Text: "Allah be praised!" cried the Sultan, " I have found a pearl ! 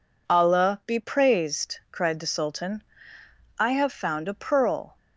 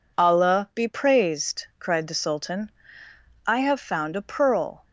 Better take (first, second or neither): neither